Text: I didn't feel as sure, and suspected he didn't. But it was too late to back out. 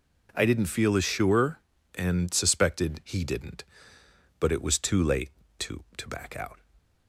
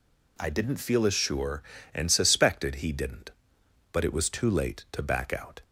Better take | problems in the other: second | says "to" twice; at 5.9 s

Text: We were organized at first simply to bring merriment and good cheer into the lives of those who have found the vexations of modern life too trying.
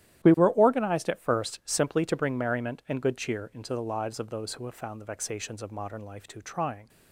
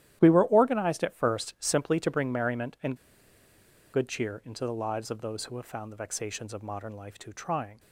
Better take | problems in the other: first | starts louder than the rest; strong; until 1.2 s; 12 dB; strong in the first // pauses between "and" and "good"; noticeable; at 2.9 s; 0.96 s long

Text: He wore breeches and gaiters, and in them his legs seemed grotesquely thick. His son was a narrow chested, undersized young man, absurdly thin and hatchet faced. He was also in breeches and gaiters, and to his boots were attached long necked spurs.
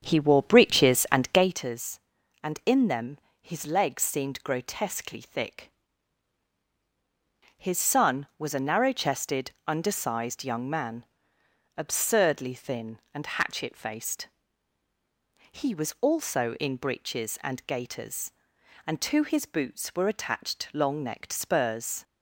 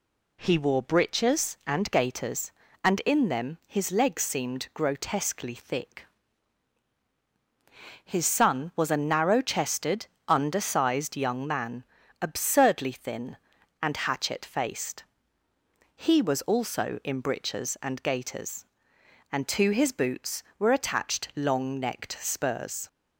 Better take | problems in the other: second | starts louder than the rest; strong; until 1.7 s; 8 dB // pauses between "them" and "his"; slight; at 3.1 s; 0.24 s long

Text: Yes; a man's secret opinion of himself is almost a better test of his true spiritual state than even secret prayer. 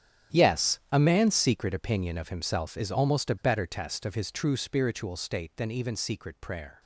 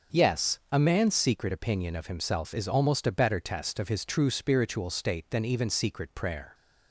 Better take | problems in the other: second | gets quieter; strong; throughout; 14.5 dB // starts louder than the rest; strong; until 1.4 s; 10.5 dB; also in the second

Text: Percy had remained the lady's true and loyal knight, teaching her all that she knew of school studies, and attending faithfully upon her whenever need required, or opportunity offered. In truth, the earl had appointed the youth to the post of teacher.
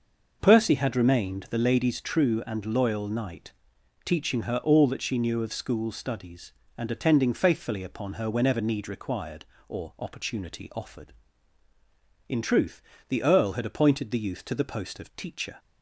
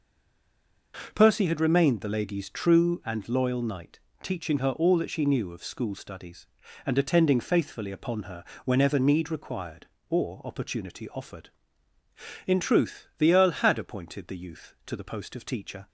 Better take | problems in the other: first | stays silent before the first word; slight; until 0.9 s; 0.9 s long // pauses between "her" and "whenever"; slight; at 8.4 s; 0.18 s long

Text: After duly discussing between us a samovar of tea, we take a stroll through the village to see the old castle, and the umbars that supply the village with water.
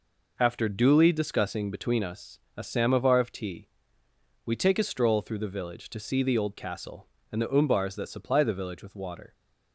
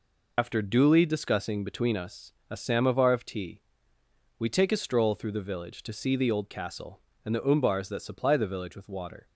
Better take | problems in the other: first | loses the start of "After"; at 0.3 s; 65 ms // pauses between "us" and "a"; slight; at 2.3 s; 0.20 s long; slight in the first

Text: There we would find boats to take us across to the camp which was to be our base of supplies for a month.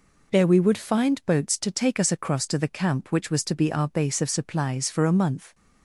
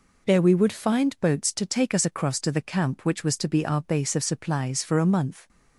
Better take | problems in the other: neither | none

